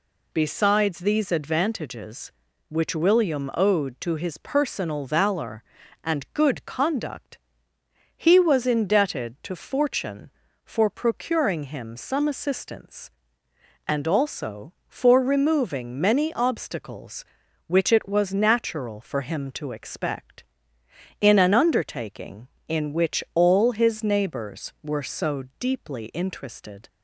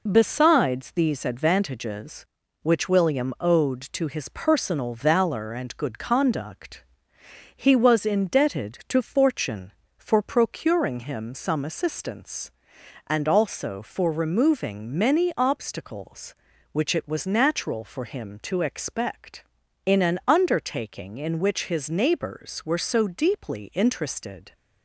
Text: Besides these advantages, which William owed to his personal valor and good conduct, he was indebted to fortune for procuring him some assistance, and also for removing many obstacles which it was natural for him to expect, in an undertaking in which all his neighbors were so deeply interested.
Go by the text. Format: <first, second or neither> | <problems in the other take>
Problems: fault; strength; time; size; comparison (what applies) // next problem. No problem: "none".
first | skips "all"; at 21.6 s